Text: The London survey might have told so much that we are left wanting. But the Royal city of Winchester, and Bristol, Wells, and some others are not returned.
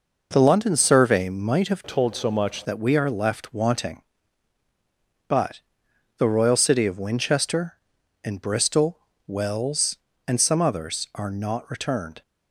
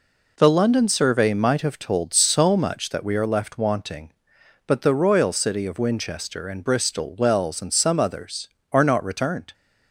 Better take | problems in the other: second | changes voice from "told" to "much"; from 1.8 to 2.6 s; 0.8 s long // pauses between "But" and "the"; noticeable; at 5.5 s; 0.58 s long

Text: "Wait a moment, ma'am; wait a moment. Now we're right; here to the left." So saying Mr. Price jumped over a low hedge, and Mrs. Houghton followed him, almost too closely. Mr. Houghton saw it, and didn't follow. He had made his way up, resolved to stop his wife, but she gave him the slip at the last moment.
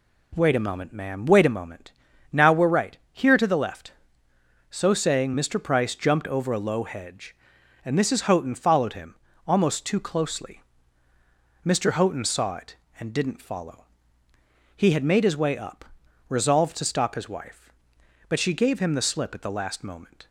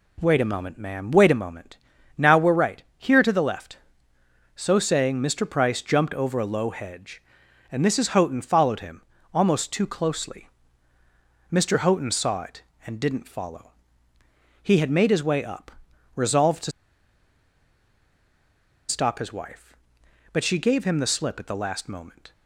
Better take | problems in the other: first | pauses between "to" and "stop"; strong; at 16.7 s; 2.1 s long

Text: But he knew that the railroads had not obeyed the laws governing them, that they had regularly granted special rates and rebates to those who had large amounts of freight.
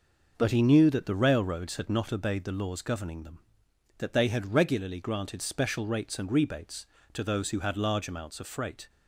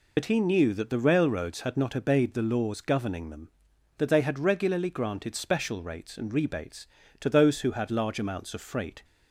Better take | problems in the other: first | loses the start of "But"; at 0.1 s; 50 ms

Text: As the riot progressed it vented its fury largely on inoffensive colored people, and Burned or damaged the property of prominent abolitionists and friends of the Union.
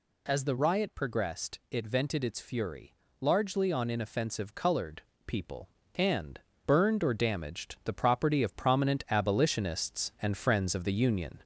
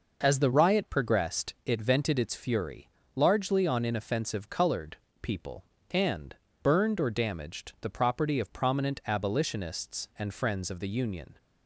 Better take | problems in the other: second | gets louder; slight; throughout; 3 dB // pauses between "fury" and "largely"; slight; at 2.9 s; 0.26 s long; slight in the second // pauses between "colored" and "people"; slight; at 5.0 s; 0.25 s long; slight in the second // pauses between "and" and "Burned"; slight; at 6.4 s; 0.26 s long; slight in the second

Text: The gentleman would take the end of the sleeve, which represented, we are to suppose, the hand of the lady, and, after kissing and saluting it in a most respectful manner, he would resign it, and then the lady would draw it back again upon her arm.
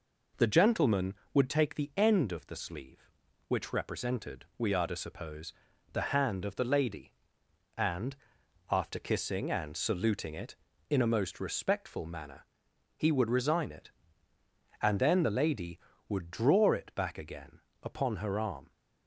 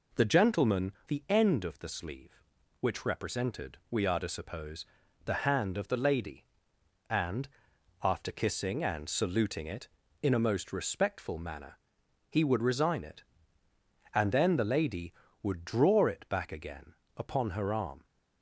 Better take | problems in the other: first | skips "would take"; at 0.9 s // pauses between "again" and "upon"; slight; at 16.9 s; 0.24 s long; slight in the first

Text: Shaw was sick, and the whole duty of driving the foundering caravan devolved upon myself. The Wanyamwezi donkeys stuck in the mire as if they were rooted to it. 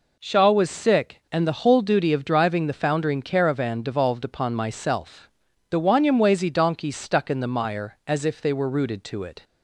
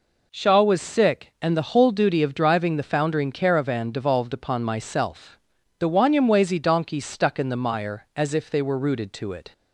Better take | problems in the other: neither | none

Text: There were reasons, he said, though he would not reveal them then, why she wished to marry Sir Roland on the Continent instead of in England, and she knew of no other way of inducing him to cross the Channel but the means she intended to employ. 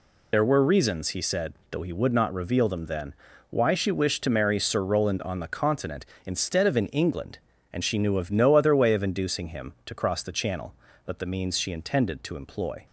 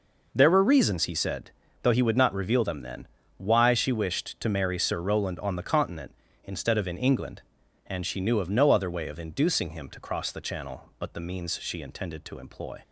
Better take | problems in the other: second | loses the start of "There"; at 0.3 s; 50 ms

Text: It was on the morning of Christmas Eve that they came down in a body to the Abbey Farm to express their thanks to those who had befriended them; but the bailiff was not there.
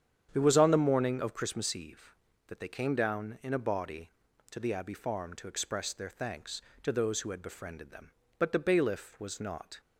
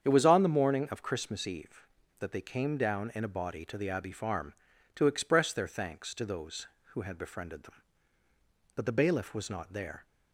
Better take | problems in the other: second | starts louder than the rest; strong; until 1.3 s; 8.5 dB; strong in the second // stops before "there"; at 9.8 s

